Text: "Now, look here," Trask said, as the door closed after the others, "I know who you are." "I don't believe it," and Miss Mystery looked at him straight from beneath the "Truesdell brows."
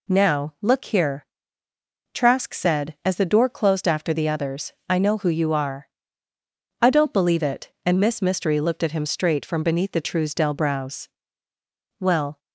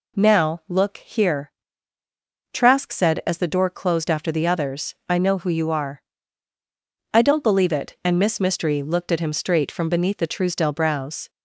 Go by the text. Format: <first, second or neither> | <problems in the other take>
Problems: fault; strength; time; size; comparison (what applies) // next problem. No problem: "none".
second | goes on to say "Well"; slight; from 11.9 s on; 0.40 s long